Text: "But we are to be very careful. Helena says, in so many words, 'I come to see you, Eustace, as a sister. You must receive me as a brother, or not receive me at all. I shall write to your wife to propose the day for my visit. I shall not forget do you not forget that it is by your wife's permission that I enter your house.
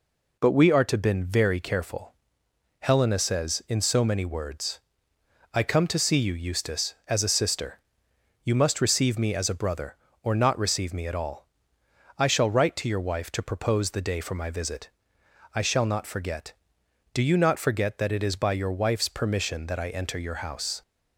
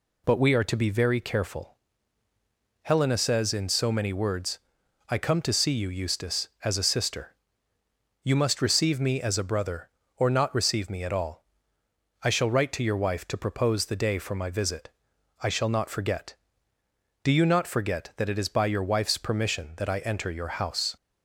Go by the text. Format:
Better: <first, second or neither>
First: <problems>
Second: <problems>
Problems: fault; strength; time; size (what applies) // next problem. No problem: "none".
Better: second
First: says "been" for "be"; at 0.9 s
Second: none